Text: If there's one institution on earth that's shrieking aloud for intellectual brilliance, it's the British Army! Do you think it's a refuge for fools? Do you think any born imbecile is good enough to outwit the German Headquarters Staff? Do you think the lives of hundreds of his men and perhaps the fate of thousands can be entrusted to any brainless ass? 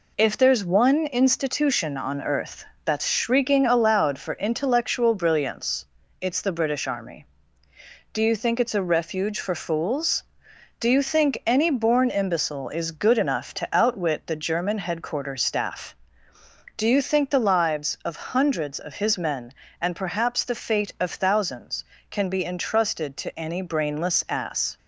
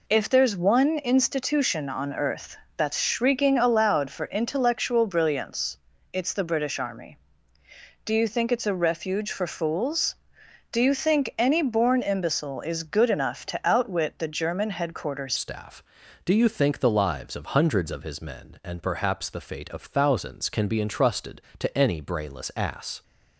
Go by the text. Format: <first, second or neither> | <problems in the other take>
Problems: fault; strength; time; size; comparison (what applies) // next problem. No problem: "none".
first | pauses between "earth" and "that's"; slight; at 2.5 s; 0.20 s long; slight in the first // changes voice at "Staff"; from 15.3 s on; 7.7 s long